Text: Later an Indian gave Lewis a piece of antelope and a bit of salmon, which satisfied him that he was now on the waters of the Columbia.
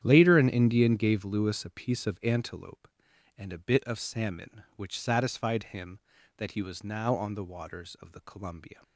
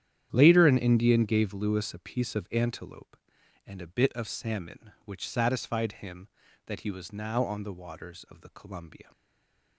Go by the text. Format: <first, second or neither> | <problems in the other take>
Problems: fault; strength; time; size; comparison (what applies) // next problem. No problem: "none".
first | starts louder than the rest; strong; until 1.3 s; 10 dB; strong in the first // stays silent after the last word; slight; from 9.1 s on; 0.6 s long